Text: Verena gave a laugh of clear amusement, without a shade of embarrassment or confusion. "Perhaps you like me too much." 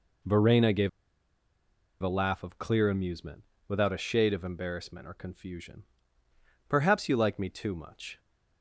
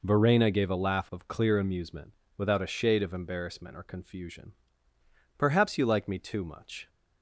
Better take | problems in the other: second | pauses between "gave" and "a"; at 0.8 s; 1.1 s long

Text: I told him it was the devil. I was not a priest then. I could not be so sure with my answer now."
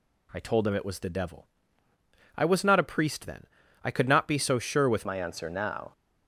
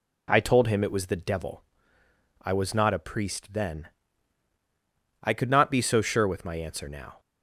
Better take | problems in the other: second | changes voice at "my"; from 5.0 s on; 0.9 s long

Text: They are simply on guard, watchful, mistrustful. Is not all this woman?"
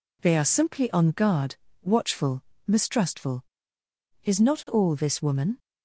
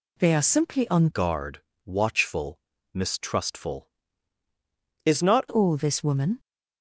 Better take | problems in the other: first | changes voice from "guard" to "not"; from 1.1 to 5.4 s; 4.3 s long

